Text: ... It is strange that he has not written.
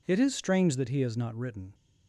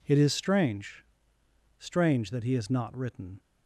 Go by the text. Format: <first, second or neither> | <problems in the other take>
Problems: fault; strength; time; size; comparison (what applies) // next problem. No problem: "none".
first | says "strange" twice; at 1.7 s